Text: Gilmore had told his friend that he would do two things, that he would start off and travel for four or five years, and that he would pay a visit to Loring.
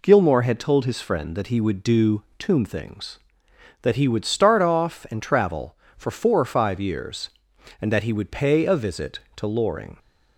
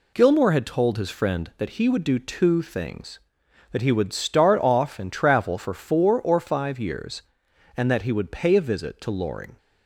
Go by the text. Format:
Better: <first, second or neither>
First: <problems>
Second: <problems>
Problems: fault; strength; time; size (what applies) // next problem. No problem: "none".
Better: second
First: says "tomb" for "two"; at 2.3 s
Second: none